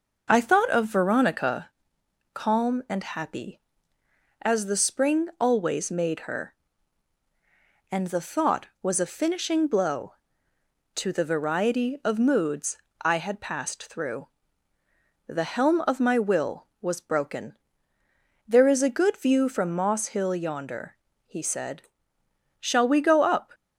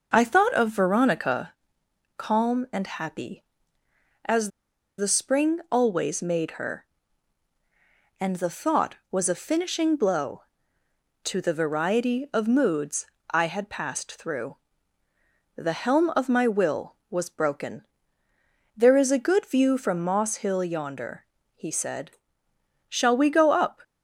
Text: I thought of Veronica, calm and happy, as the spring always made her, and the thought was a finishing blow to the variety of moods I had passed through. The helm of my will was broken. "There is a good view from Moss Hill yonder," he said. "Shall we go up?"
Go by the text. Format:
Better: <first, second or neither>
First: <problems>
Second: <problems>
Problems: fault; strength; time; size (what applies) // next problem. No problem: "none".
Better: first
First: pauses between "moods" and "I"; slight; at 12.7 s; 0.26 s long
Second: pauses between "as" and "the"; noticeable; at 4.5 s; 0.48 s long // pauses between "moods" and "I"; slight; at 13.0 s; 0.26 s long